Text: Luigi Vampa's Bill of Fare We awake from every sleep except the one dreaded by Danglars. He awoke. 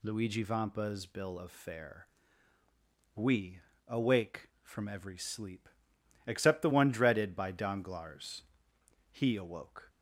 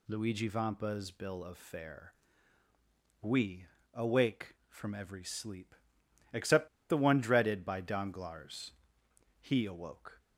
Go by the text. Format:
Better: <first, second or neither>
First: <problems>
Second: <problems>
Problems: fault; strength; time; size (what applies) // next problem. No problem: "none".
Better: first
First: pauses between "Fare" and "We"; at 2.0 s; 1.0 s long // pauses between "We" and "awake"; slight; at 3.5 s; 0.26 s long // pauses between "sleep" and "except"; noticeable; at 5.6 s; 0.58 s long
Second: pauses between "Fare" and "We"; at 2.1 s; 1.0 s long // pauses between "We" and "awake"; slight; at 3.6 s; 0.26 s long // pauses between "sleep" and "except"; noticeable; at 5.7 s; 0.58 s long // pauses between "except" and "the"; slight; at 6.6 s; 0.21 s long